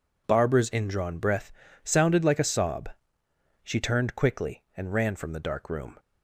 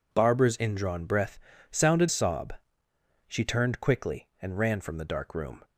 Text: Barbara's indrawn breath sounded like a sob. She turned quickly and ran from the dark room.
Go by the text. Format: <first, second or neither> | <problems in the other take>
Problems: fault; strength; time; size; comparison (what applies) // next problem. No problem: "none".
first | pauses between "breath" and "sounded"; slight; at 1.3 s; 0.32 s long; slight in the first // skips "like a"; at 2.0 s